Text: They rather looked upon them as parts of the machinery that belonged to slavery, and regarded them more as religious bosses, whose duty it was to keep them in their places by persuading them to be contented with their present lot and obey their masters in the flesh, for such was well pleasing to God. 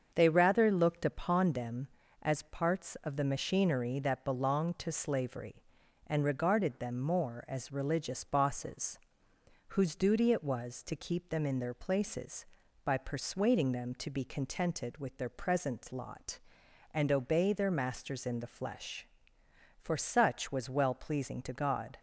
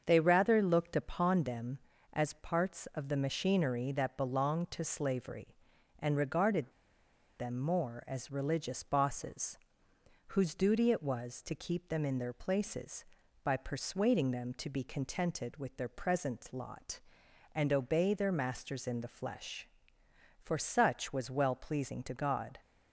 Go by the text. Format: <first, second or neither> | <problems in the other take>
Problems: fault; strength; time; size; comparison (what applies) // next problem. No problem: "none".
first | starts louder than the rest; until 1.0 s; 7 dB; also in the first // pauses between "regarded" and "them"; noticeable; at 6.7 s; 0.67 s long